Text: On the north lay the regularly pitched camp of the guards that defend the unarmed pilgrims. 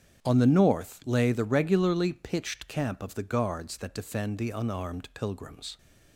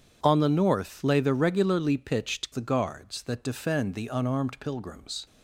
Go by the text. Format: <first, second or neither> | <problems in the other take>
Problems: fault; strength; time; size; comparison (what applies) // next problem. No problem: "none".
first | starts louder than the rest; strong; until 1.2 s; 8 dB; strong in the first // skips "camp of"; at 2.5 s